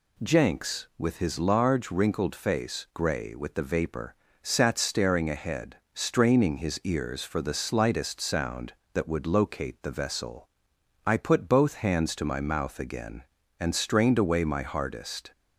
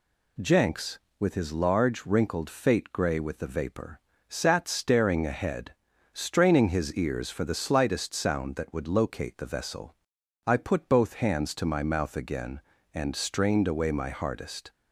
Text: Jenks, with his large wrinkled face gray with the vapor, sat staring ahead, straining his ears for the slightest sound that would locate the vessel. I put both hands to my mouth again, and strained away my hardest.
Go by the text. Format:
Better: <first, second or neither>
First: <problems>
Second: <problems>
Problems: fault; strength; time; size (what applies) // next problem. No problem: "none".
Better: first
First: none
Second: says "fate" for "face"; at 2.4 s